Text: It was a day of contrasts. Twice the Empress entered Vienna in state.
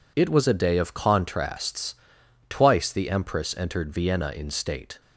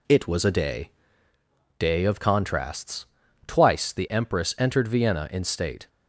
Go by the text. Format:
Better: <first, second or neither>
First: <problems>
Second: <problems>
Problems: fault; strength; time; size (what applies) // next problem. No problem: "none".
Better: first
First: none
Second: says "day" twice; at 1.7 s